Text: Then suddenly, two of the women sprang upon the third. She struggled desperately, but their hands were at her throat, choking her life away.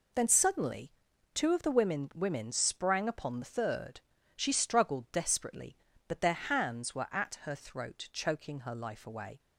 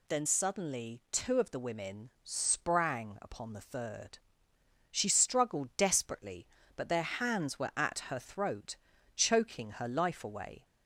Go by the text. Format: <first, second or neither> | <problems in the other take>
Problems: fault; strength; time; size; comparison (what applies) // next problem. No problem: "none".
second | says "women" twice; at 2.1 s